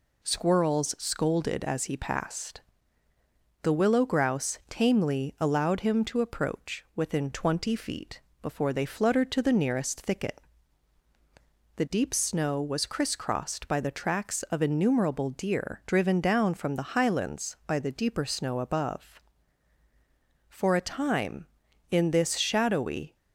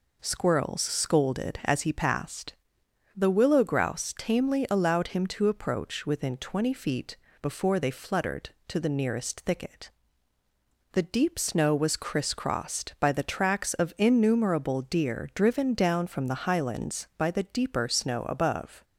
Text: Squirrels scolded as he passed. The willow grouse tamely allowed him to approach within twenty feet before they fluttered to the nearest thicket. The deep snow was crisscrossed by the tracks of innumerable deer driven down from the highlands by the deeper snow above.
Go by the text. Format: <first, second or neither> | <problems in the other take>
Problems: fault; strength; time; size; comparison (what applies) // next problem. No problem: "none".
second | pauses between "feet" and "before"; slight; at 8.2 s; 0.20 s long; slight in the second // goes on to say "For a time in this shadowy"; strong; from 20.4 s on; 2.6 s long